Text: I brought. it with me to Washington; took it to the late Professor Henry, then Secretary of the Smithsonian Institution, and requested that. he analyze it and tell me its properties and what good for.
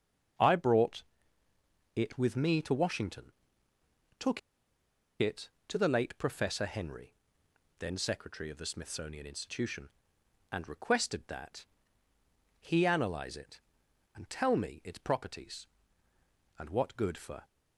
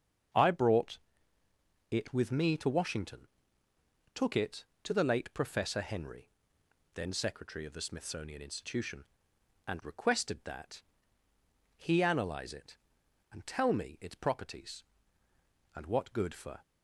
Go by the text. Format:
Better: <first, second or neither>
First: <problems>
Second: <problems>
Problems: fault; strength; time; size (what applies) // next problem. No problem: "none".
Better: second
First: starts louder than the rest; strong; until 2.3 s; 7.5 dB // pauses between "took" and "it"; noticeable; at 4.3 s; 0.81 s long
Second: starts louder than the rest; strong; until 2.2 s; 7.5 dB